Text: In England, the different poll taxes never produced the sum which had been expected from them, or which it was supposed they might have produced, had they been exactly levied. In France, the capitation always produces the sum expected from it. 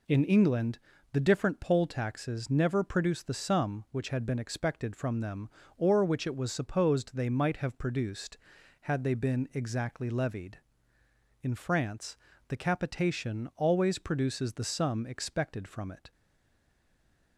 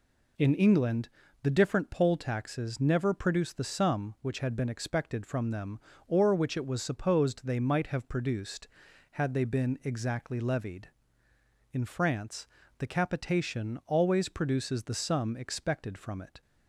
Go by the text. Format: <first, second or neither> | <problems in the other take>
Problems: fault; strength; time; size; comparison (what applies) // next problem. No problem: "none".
second | stays silent after the last word; noticeable; from 16.1 s on; 1.2 s long